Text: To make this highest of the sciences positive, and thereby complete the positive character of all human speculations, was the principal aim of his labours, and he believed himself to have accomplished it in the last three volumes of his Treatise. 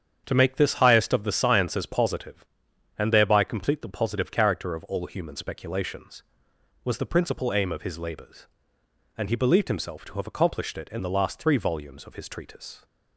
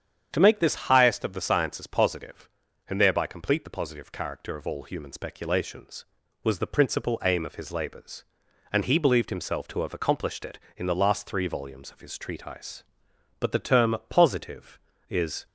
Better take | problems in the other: first | starts louder than the rest; strong; until 1.3 s; 8.5 dB; strong in the first // goes on to say "But the term Positive is"; strong; from 13.4 s on; 2.0 s long

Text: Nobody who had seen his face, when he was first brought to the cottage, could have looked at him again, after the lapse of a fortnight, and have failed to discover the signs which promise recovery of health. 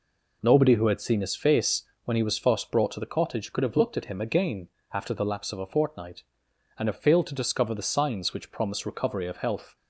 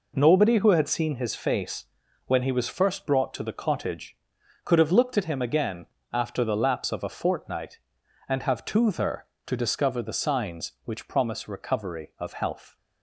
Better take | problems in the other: first | says "toother" for "failed"; at 8.6 s

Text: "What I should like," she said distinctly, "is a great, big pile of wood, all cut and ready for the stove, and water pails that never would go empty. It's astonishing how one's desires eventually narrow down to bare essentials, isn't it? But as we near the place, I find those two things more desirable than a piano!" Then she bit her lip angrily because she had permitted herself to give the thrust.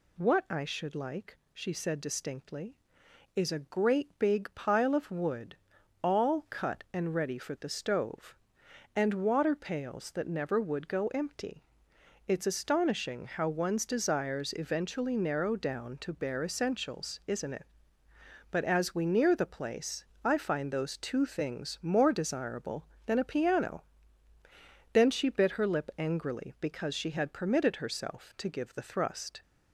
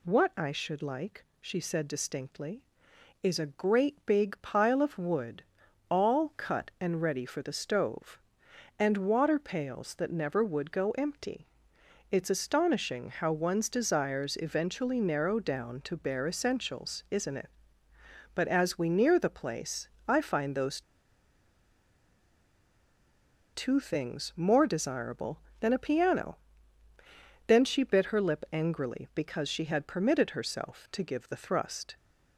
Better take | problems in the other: first | pauses between "those" and "two"; strong; at 20.8 s; 2.7 s long

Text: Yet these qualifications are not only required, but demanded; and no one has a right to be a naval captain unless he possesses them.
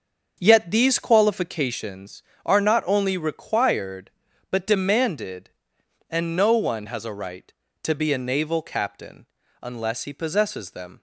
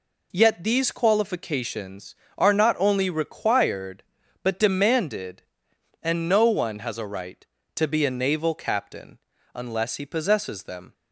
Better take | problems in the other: second | starts louder than the rest; until 1.9 s; 7 dB // pauses between "captain" and "unless"; slight; at 9.2 s; 0.36 s long; slight in the second

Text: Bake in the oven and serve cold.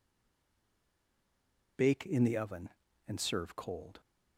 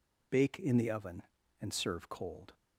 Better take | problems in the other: second | stays silent before the first word; noticeable; until 1.7 s; 1.7 s long

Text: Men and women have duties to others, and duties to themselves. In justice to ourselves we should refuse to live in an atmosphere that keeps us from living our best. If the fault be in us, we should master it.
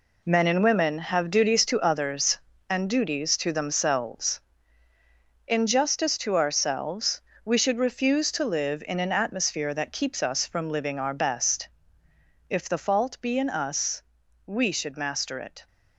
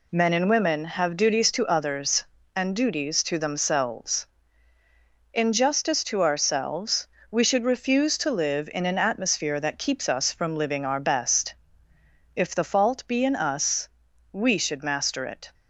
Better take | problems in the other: second | gets quieter; strong; throughout; 9.5 dB // pauses between "ourselves" and "we"; slight; at 7.2 s; 0.24 s long; slight in the second

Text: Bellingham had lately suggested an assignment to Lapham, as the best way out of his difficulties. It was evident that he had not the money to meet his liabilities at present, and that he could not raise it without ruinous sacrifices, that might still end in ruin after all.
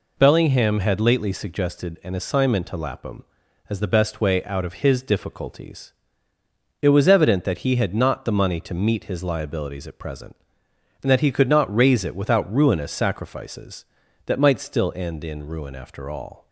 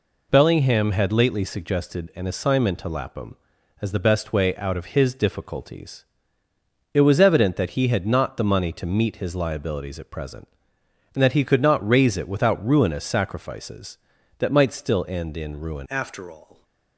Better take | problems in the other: first | changes voice at "after"; from 15.8 s on; 0.8 s long

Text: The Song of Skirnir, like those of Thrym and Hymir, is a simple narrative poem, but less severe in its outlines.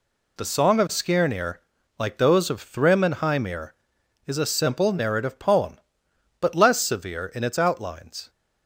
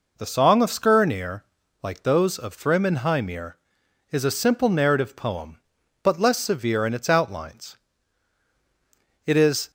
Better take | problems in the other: first | goes on to say "It is"; slight; from 9.2 s on; 0.44 s long

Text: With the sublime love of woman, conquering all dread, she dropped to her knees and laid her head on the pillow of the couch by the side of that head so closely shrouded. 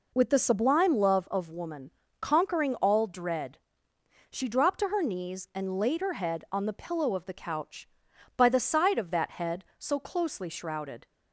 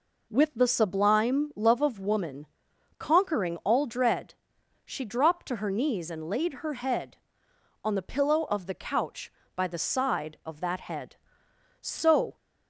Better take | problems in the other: first | stops before "closely shrouded"; at 12.3 s

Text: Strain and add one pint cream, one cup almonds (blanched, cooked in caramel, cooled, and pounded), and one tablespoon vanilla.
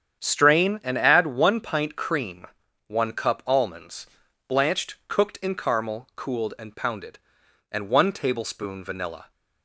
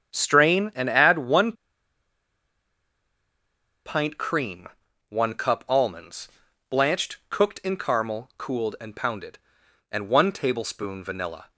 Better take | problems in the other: first | starts louder than the rest; strong; until 1.1 s; 8 dB; strong in the first // pauses between "one" and "pint"; strong; at 1.5 s; 2.3 s long

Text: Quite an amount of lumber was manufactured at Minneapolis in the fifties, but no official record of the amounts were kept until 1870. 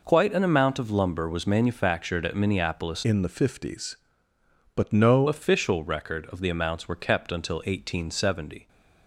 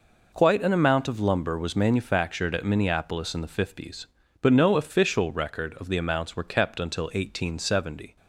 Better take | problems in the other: second | changes voice from "in" to "no"; from 3.0 to 5.2 s; 2.2 s long

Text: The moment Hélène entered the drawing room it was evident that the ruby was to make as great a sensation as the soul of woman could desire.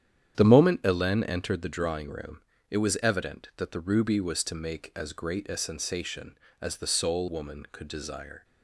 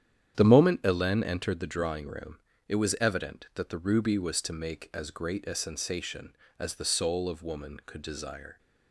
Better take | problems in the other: second | starts louder than the rest; strong; until 1.3 s; 9.5 dB; strong in the second // pauses between "room" and "it"; slight; at 2.3 s; 0.30 s long; slight in the second // skips "of"; at 7.2 s

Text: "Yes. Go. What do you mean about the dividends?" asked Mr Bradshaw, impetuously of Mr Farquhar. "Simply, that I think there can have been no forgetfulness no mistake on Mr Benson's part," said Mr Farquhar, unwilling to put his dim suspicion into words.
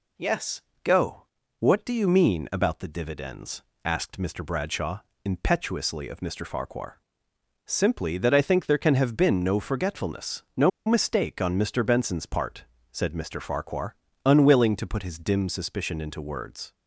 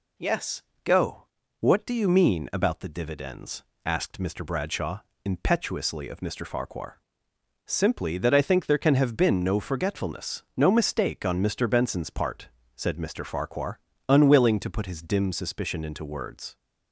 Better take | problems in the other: second | pauses between "no" and "mistake"; slight; at 10.6 s; 0.16 s long

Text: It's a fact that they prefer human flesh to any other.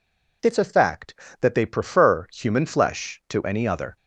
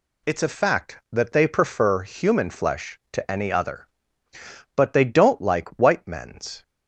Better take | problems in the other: first | goes on to say "But they don't like white men's"; strong; from 4.7 s on; 1.8 s long

